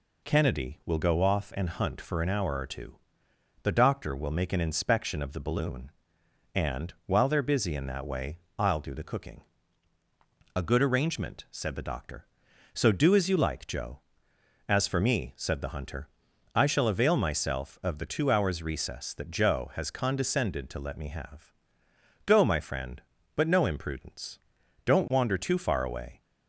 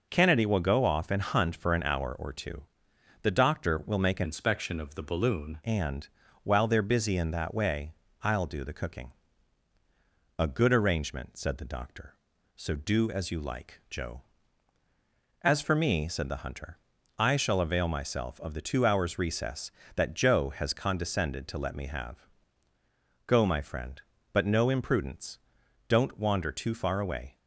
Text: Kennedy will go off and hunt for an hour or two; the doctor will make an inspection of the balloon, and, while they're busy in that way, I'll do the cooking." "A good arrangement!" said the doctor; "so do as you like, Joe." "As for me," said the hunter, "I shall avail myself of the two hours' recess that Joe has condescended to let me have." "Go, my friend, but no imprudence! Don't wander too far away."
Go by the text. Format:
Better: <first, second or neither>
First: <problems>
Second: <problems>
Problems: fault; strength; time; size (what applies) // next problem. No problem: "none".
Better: first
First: none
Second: changes voice from "inspection" to "balloon"; from 4.2 to 5.6 s; 1.4 s long